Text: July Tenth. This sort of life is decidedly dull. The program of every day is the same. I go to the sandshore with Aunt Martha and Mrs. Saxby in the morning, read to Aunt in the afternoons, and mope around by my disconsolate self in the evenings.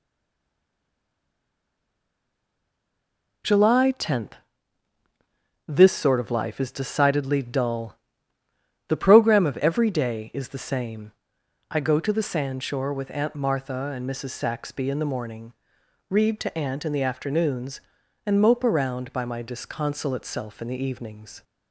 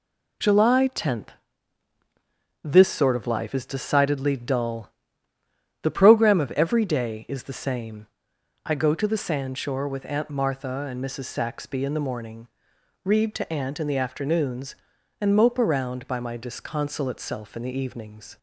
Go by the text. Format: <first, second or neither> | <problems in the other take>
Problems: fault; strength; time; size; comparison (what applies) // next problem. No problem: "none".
second | stays silent before the first word; strong; until 3.4 s; 3.4 s long